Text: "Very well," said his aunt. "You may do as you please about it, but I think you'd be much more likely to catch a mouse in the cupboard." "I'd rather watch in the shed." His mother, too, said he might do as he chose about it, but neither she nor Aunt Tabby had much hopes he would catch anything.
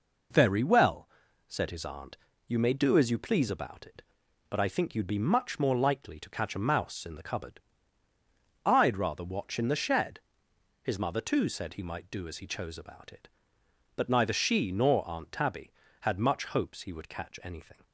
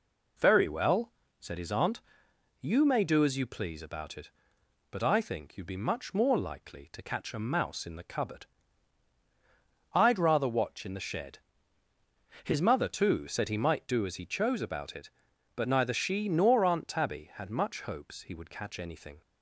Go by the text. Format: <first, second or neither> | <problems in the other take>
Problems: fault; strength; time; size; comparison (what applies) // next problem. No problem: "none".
neither | none